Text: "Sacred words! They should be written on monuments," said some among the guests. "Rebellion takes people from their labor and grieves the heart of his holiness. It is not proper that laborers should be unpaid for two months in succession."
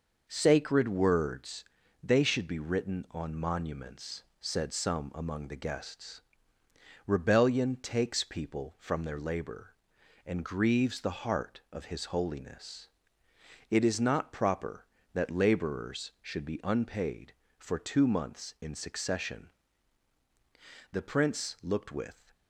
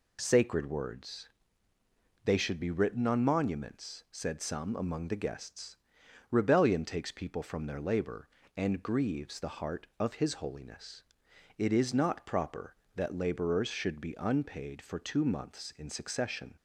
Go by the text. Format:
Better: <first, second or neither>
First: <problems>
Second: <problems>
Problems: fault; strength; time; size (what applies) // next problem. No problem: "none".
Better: second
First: goes on to say "The prince looked with"; from 20.9 s on; 1.4 s long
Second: none